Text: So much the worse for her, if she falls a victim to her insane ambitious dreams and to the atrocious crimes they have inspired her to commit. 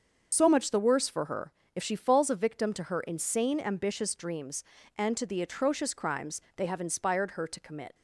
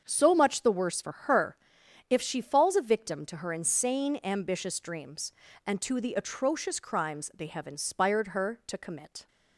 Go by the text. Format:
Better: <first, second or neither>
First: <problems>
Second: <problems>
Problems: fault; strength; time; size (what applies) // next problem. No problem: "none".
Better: second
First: loses the start of "So"; at 0.3 s; 40 ms // starts louder than the rest; until 1.3 s; 6.5 dB // pauses between "crimes" and "they"; slight; at 6.4 s; 0.16 s long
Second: starts louder than the rest; strong; until 1.0 s; 7 dB